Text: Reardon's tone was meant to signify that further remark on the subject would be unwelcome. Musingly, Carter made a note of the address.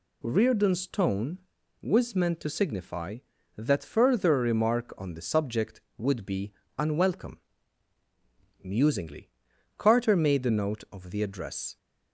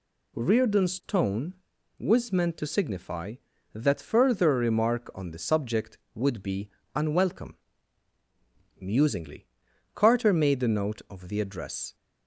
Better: neither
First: pauses between "be" and "unwelcome"; slight; at 6.5 s; 0.26 s long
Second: pauses between "be" and "unwelcome"; slight; at 6.6 s; 0.26 s long

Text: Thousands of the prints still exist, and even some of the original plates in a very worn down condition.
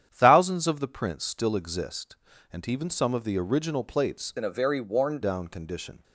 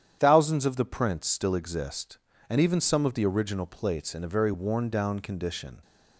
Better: second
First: starts louder than the rest; strong; until 1.1 s; 9.5 dB // changes voice from "in" to "worn"; from 4.3 to 5.1 s; 0.8 s long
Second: starts louder than the rest; strong; until 1.2 s; 9.5 dB

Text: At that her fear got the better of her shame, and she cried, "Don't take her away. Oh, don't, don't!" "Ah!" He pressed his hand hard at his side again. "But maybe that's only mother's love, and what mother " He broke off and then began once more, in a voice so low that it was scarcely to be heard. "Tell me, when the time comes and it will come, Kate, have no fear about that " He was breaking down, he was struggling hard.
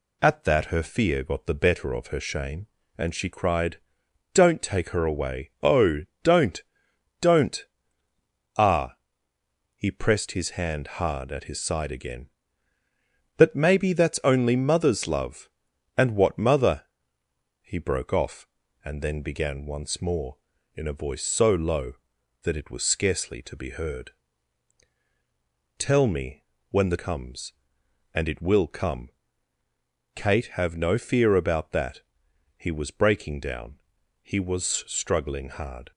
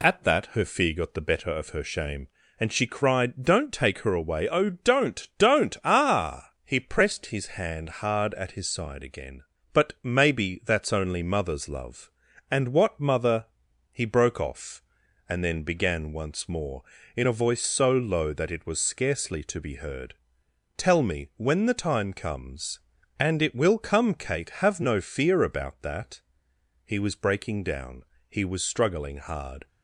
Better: second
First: skips "time"; at 26.9 s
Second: none

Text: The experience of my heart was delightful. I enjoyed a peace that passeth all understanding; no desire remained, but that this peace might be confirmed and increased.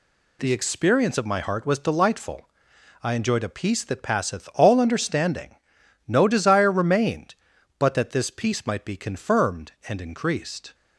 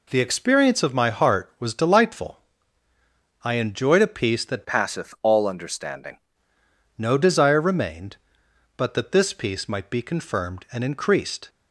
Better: first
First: none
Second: changes voice from "passeth" to "understanding"; from 4.6 to 6.1 s; 1.5 s long

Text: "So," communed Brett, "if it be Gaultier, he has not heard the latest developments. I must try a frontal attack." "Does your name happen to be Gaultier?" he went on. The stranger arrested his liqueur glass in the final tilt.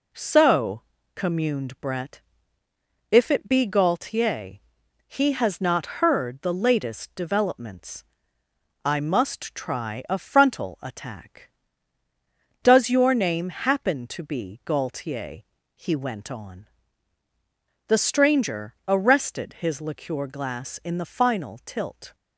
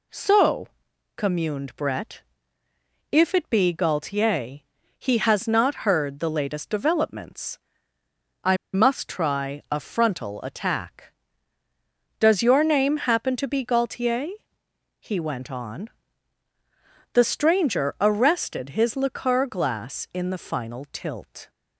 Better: first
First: none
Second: pauses between "I" and "must"; slight; at 8.5 s; 0.17 s long

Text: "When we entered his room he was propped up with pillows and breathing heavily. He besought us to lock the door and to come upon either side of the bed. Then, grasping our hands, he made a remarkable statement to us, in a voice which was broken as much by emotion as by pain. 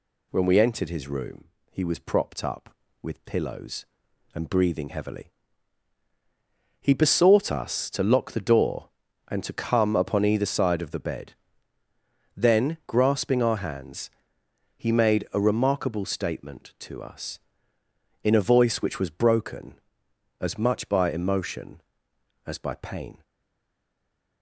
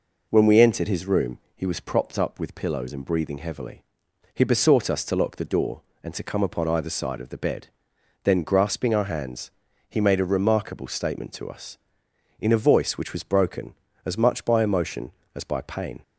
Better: second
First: pauses between "room" and "he"; slight; at 1.4 s; 0.26 s long // stays silent after the last word; noticeable; from 23.2 s on; 1.2 s long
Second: pauses between "room" and "he"; slight; at 1.3 s; 0.18 s long

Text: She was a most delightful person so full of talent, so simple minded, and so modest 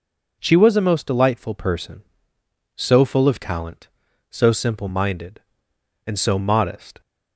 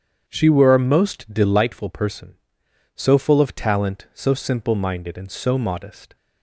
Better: first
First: none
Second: starts louder than the rest; strong; until 1.2 s; 8 dB // says "were" for "was"; at 0.4 s

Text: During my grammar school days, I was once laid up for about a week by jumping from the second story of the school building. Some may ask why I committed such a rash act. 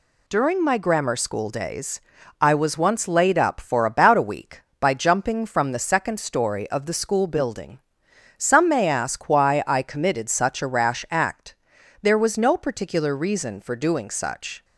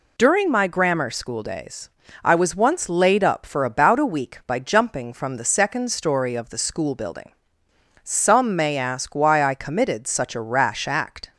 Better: second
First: goes on to say "There was no particular reason for doing such"; strong; from 12.0 s on; 2.6 s long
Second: none

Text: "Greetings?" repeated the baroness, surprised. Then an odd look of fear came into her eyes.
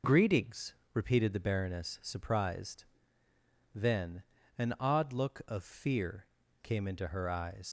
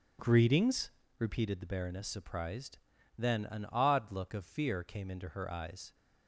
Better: second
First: pauses between "Then" and "an"; slight; at 4.2 s; 0.34 s long // pauses between "fear" and "came"; slight; at 6.2 s; 0.34 s long // leaves "eyes" unfinished; at 7.6 s; 110 ms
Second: none

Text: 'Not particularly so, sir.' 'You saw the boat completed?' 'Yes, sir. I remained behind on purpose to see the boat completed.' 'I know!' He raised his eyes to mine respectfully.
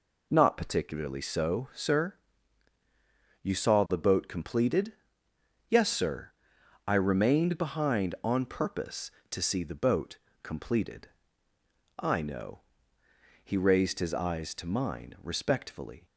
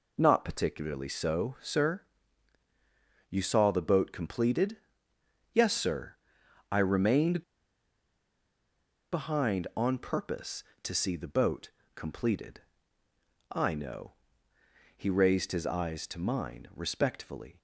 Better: first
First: pauses between "boat" and "completed"; slight; at 10.1 s; 0.24 s long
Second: pauses between "remained" and "behind"; strong; at 7.4 s; 1.7 s long // pauses between "boat" and "completed"; slight; at 11.6 s; 0.24 s long

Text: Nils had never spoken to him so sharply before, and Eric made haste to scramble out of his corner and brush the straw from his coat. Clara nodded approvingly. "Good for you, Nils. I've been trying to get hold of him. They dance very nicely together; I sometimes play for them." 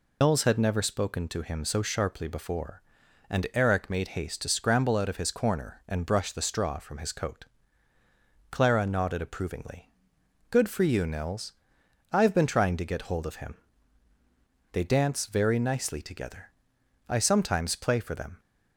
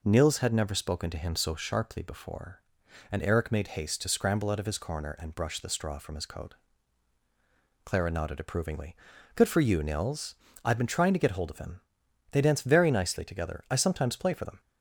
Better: second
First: loses the start of "Nils"; at 0.2 s; 110 ms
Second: none

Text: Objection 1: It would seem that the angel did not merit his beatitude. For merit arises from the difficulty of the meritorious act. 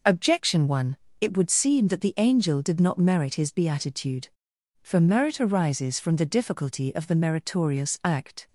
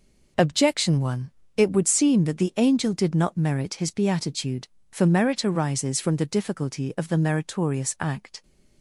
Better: neither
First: none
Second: none

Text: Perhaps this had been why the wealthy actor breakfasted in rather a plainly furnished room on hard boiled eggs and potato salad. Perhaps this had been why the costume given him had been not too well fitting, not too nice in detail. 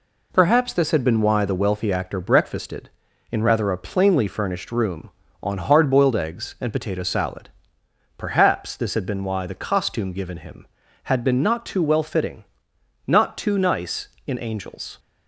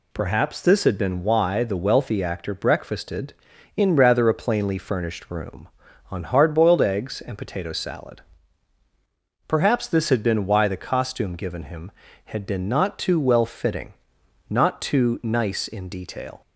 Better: second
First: says "angels" for "detail"; at 14.3 s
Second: none

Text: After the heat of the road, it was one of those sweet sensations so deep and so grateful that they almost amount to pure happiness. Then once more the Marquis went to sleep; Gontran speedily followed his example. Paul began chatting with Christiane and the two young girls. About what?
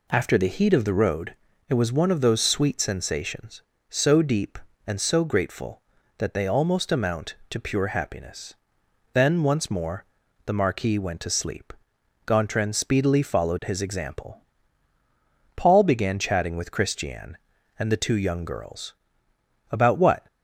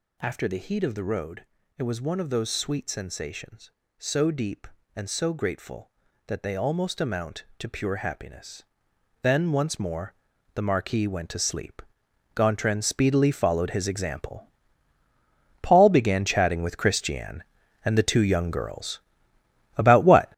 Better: first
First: pauses between "more" and "the"; at 10.0 s; 0.40 s long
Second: gets louder; strong; throughout; 8.5 dB // pauses between "more" and "the"; at 10.1 s; 0.40 s long

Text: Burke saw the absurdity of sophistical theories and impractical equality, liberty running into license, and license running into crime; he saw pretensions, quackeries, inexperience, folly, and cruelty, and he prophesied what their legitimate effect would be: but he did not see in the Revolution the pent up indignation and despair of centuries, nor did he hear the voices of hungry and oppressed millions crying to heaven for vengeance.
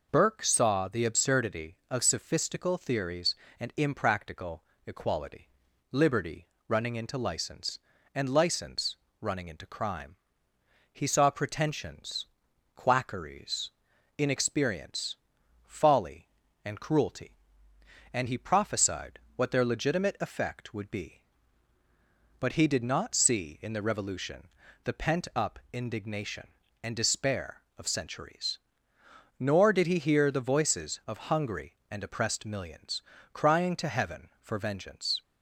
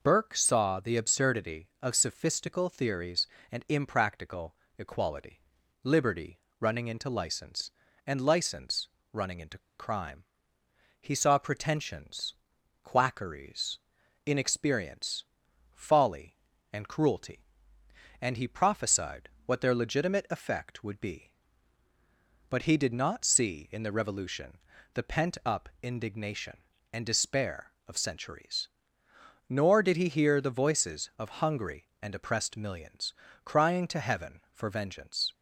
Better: first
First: pauses between "impractical" and "equality"; slight; at 4.6 s; 0.24 s long // pauses between "liberty" and "running"; slight; at 6.4 s; 0.20 s long // pauses between "license" and "running"; slight; at 8.9 s; 0.24 s long // pauses between "prophesied" and "what"; slight; at 19.1 s; 0.16 s long // pauses between "Revolution" and "the"; at 24.4 s; 0.38 s long // pauses between "millions" and "crying"; slight; at 33.0 s; 0.32 s long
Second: pauses between "impractical" and "equality"; slight; at 4.5 s; 0.24 s long // pauses between "liberty" and "running"; slight; at 6.3 s; 0.20 s long // pauses between "license" and "running"; slight; at 8.8 s; 0.24 s long // pauses between "into" and "crime"; slight; at 9.5 s; 0.18 s long // pauses between "prophesied" and "what"; slight; at 19.2 s; 0.16 s long // pauses between "Revolution" and "the"; at 24.5 s; 0.38 s long // pauses between "millions" and "crying"; slight; at 33.1 s; 0.32 s long

